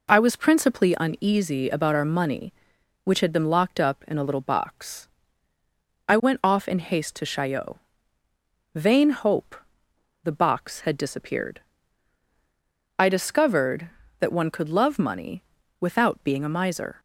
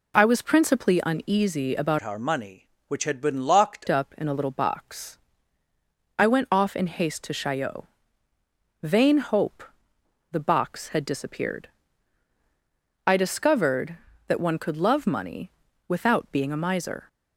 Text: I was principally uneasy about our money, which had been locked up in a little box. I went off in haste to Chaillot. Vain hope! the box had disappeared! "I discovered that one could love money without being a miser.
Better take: first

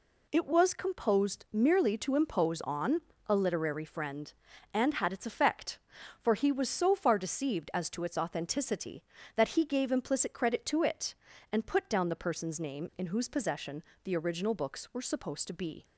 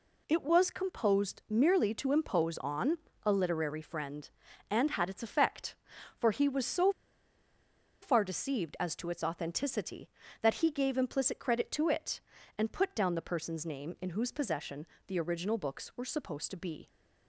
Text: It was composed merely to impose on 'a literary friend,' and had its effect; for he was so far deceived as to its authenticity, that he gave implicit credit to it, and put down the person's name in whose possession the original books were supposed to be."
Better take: first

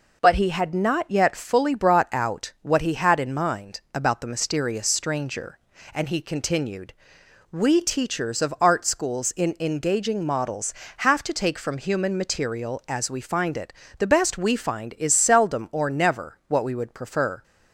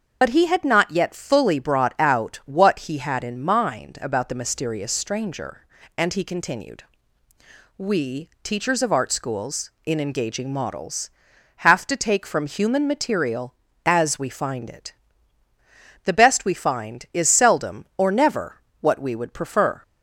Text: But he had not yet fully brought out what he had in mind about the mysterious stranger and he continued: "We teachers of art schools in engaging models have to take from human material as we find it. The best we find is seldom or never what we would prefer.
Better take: first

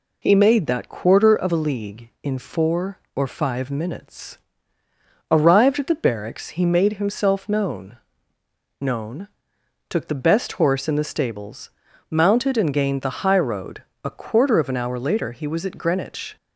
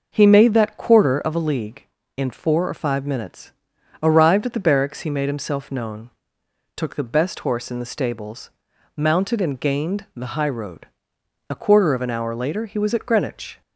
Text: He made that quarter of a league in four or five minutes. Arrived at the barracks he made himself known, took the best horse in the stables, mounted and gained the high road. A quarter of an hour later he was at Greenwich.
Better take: second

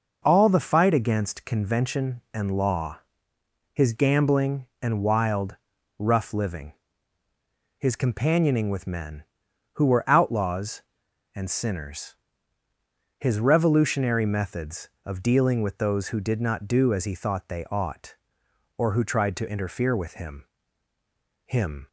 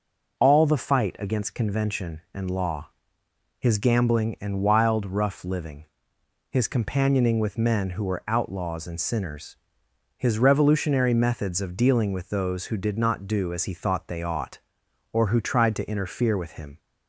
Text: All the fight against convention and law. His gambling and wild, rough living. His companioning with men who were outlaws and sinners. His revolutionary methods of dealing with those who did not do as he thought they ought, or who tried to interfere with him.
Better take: second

